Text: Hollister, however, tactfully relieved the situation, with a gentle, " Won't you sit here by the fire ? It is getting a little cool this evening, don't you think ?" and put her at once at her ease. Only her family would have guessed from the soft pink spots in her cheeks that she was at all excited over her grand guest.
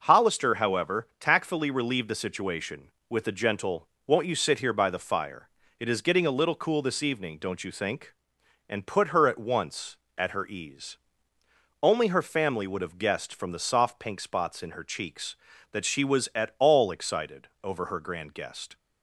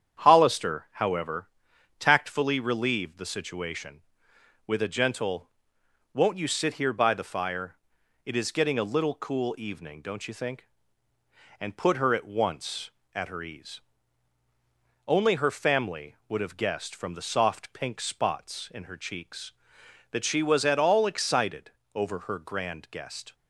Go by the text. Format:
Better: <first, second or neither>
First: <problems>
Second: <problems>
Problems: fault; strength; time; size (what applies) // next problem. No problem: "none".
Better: first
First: starts louder than the rest; until 1.0 s; 6.5 dB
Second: starts louder than the rest; strong; until 1.2 s; 8.5 dB // skips "this"; at 9.5 s // pauses between "excited" and "over"; slight; at 21.7 s; 0.24 s long